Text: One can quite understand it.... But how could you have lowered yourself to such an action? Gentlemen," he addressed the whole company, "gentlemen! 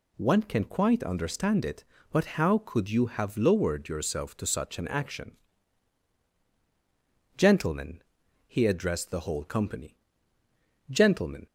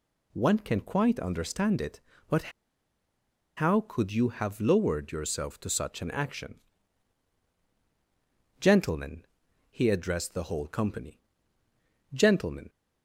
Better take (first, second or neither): first